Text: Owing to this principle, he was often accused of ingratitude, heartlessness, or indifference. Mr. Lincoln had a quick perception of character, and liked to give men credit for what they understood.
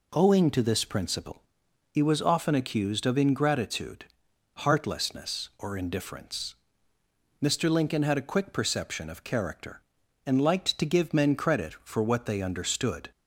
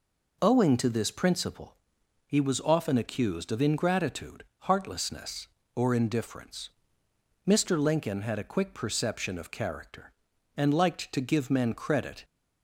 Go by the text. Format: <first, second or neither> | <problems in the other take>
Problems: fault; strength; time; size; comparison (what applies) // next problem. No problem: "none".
first | stops before "for what they understood"; at 12.2 s